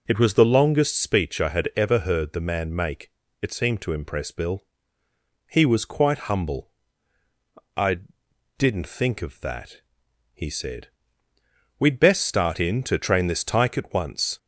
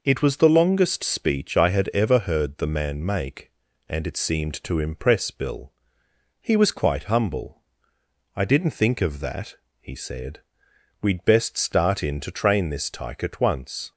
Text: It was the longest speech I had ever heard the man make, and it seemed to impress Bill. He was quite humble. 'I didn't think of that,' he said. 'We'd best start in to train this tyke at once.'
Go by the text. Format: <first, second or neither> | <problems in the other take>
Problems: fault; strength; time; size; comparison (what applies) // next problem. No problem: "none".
second | skips "and"; at 3.2 s // pauses between "I" and "didn't"; noticeable; at 7.9 s; 0.60 s long